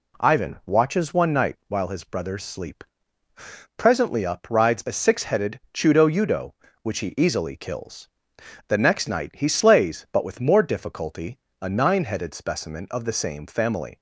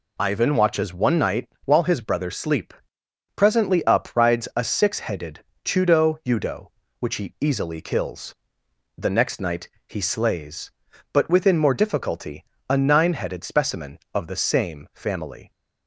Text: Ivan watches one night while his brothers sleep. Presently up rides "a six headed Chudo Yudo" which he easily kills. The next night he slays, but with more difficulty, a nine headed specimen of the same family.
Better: first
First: none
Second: pauses between "night" and "while"; slight; at 1.4 s; 0.16 s long // pauses between "headed" and "Chudo"; slight; at 5.3 s; 0.24 s long // pauses between "night" and "he"; slight; at 9.6 s; 0.20 s long // says "within" for "with"; at 11.2 s

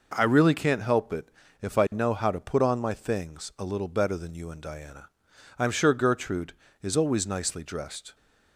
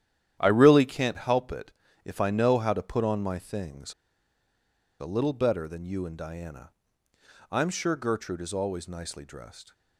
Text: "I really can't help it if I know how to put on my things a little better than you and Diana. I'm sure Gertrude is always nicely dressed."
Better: first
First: pauses between "it" and "if"; slight; at 1.3 s; 0.32 s long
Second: starts louder than the rest; strong; until 1.4 s; 10.5 dB // pauses between "it" and "if"; slight; at 1.7 s; 0.32 s long // pauses between "things" and "a"; at 3.9 s; 1.0 s long

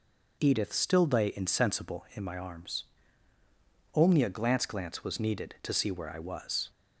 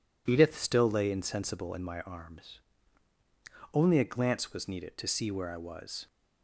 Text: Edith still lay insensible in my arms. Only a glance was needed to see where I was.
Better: second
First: says "glance" twice; at 4.6 s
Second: none

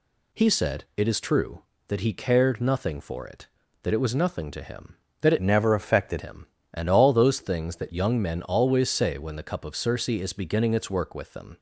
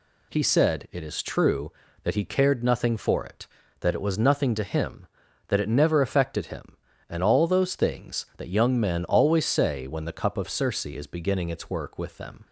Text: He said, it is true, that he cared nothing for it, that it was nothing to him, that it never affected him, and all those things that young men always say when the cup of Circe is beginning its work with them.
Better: second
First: changes voice from "never" to "affected"; from 5.4 to 6.2 s; 0.8 s long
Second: none

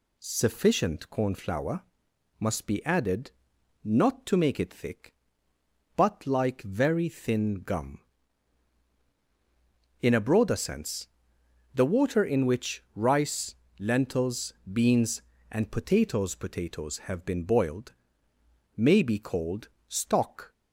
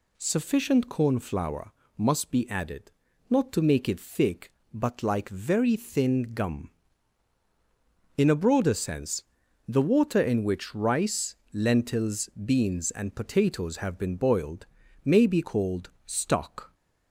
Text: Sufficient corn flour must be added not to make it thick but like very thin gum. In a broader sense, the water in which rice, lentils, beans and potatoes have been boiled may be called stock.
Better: second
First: pauses between "flour" and "must"; noticeable; at 1.8 s; 0.56 s long // pauses between "added" and "not"; noticeable; at 3.3 s; 0.52 s long // says "potatoes" twice; at 16.3 s // pauses between "boiled" and "may"; noticeable; at 17.9 s; 0.83 s long // pauses between "called" and "stock"; slight; at 19.6 s; 0.20 s long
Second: pauses between "flour" and "must"; slight; at 1.7 s; 0.26 s long // pauses between "added" and "not"; at 2.9 s; 0.38 s long // pauses between "boiled" and "may"; at 14.6 s; 0.38 s long // pauses between "called" and "stock"; slight; at 15.9 s; 0.16 s long

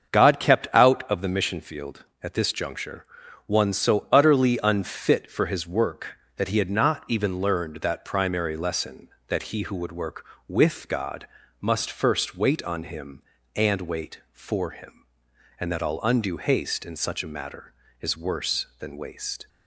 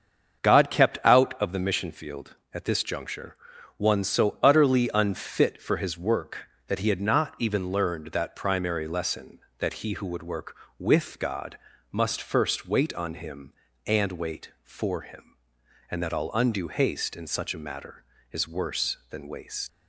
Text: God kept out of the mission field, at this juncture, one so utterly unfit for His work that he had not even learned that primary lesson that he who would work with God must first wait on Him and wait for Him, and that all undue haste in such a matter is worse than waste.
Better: first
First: starts louder than the rest; until 1.1 s; 7 dB // pauses between "God" and "must"; slight; at 11.2 s; 0.34 s long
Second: starts louder than the rest; until 1.4 s; 7 dB // pauses between "God" and "must"; slight; at 11.5 s; 0.34 s long // leaves "waste" unfinished; at 19.6 s; 90 ms

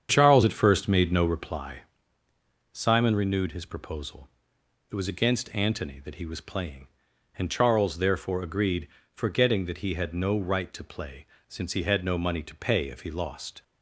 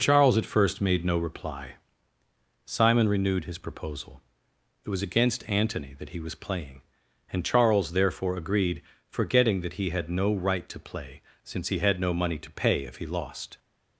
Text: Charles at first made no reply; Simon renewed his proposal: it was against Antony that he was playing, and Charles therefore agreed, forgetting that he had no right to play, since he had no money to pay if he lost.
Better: second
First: starts louder than the rest; strong; until 1.6 s; 8 dB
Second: none

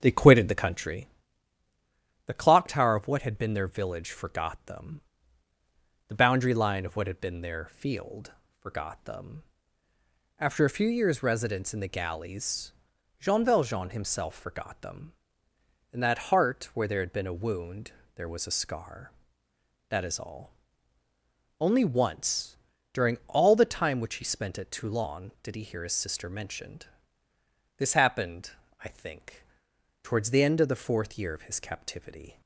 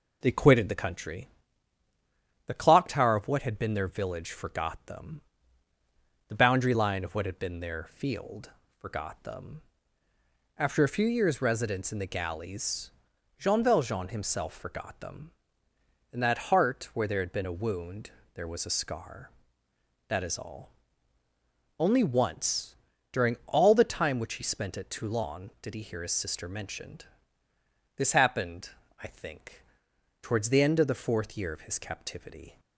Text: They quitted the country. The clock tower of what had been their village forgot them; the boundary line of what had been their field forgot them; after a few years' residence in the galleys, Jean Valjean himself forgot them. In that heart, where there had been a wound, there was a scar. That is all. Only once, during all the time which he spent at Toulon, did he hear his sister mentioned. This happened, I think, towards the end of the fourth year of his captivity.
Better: second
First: starts louder than the rest; strong; until 1.0 s; 7.5 dB // pauses between "field" and "forgot"; slight; at 8.3 s; 0.26 s long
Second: pauses between "field" and "forgot"; slight; at 8.5 s; 0.26 s long

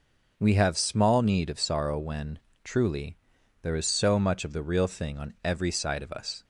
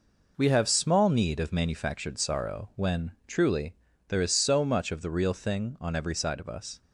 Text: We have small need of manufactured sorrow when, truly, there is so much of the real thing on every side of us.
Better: second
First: skips "manufactured"; at 1.5 s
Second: none

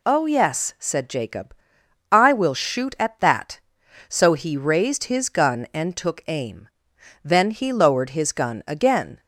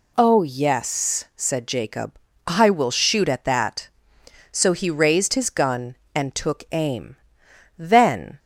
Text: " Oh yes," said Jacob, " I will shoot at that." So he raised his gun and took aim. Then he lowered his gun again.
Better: first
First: none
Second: stops before "he lowered his gun again"; at 8.3 s

